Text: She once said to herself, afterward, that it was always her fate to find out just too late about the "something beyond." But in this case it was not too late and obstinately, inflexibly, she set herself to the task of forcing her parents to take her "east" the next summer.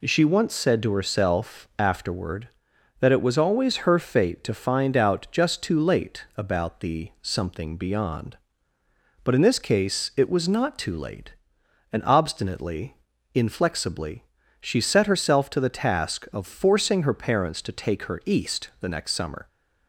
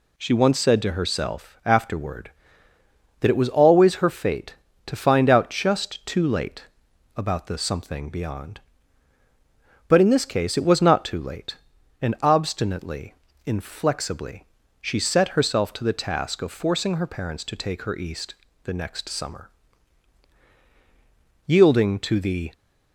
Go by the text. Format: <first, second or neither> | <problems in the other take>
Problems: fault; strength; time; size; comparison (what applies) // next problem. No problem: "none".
first | pauses between "late" and "about"; noticeable; at 6.6 s; 0.52 s long // pauses between "east" and "the"; slight; at 18.3 s; 0.30 s long // goes on to say "Yielding to the"; noticeable; from 21.4 s on; 1.0 s long